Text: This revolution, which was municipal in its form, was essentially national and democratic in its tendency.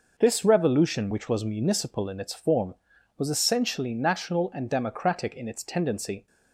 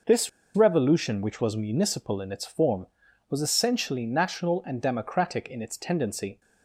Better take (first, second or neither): first